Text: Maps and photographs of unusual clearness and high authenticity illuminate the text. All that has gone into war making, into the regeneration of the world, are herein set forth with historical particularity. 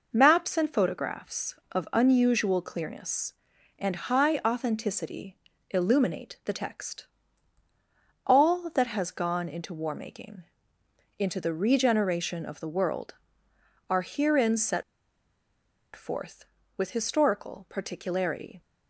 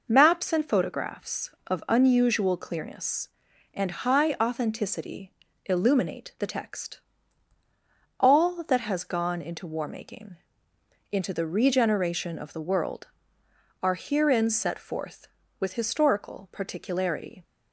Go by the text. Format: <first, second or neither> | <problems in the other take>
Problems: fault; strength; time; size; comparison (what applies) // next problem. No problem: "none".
second | pauses between "authenticity" and "illuminate"; slight; at 5.3 s; 0.32 s long; slight in the second // pauses between "set" and "forth"; at 14.8 s; 1.1 s long